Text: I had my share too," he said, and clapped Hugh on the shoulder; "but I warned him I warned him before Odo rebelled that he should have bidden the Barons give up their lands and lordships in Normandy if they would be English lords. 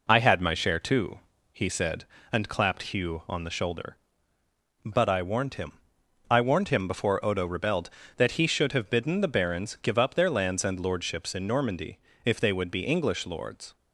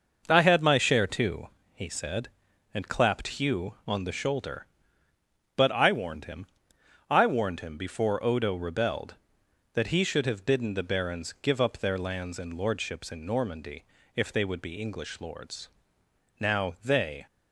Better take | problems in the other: first | pauses between "him" and "I"; noticeable; at 6.4 s; 0.64 s long; noticeable in the first // pauses between "Normandy" and "if"; slight; at 13.8 s; 0.30 s long; slight in the first // goes on to say "Now they"; noticeable; from 16.3 s on; 0.86 s long

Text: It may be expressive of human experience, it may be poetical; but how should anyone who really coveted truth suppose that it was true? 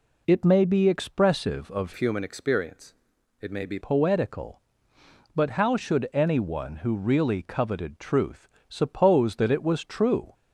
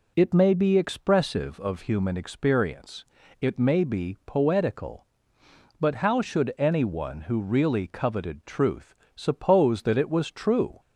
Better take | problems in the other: second | changes voice from "human" to "be"; from 1.9 to 3.7 s; 1.8 s long // pauses between "truth" and "suppose"; slight; at 8.4 s; 0.20 s long; slight in the second

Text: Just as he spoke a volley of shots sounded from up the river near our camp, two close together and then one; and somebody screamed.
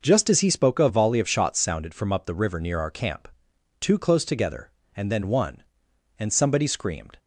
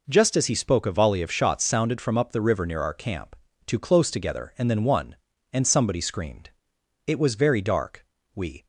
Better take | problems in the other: first | goes on to say "It was very dark We"; from 7.0 s on; 1.5 s long

